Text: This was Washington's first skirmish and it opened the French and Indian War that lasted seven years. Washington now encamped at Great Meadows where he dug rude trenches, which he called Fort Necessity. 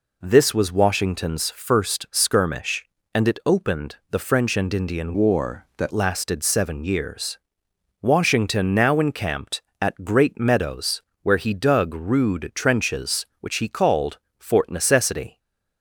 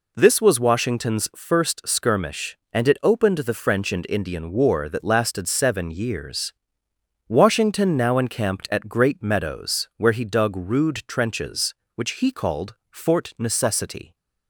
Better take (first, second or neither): second